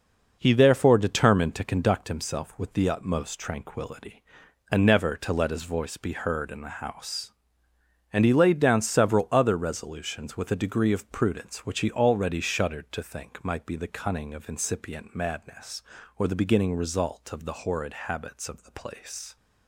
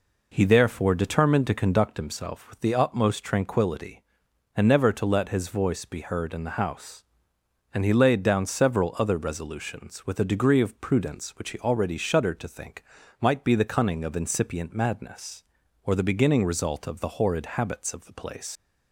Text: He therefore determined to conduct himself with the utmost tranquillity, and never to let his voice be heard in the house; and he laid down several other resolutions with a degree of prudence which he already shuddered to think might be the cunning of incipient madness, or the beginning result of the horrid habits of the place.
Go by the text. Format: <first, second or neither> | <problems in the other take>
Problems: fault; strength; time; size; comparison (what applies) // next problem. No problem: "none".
first | pauses between "think" and "might"; at 12.8 s; 0.38 s long // leaves "place" unfinished; at 18.5 s; 110 ms